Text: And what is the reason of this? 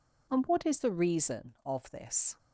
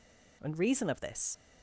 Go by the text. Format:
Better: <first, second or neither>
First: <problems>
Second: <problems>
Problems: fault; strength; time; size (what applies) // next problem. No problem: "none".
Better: first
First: none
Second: skips "what is the"; at 0.5 s